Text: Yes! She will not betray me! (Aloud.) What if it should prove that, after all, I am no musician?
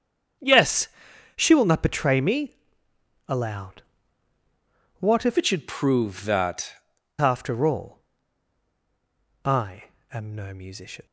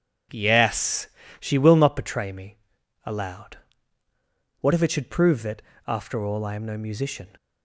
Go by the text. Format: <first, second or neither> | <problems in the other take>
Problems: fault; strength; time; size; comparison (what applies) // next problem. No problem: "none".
second | starts louder than the rest; strong; until 1.8 s; 7.5 dB // changes voice from "it" to "that"; from 5.3 to 6.7 s; 1.4 s long // pauses between "I" and "am"; slight; at 9.8 s; 0.26 s long